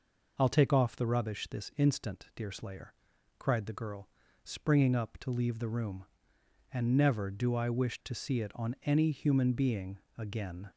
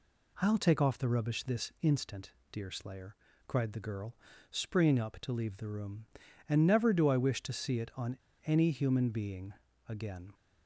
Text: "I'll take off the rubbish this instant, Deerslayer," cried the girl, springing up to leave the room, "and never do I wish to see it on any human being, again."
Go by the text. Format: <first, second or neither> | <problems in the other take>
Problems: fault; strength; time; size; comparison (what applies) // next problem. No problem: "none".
first | pauses between "on" and "any"; slight; at 8.1 s; 0.28 s long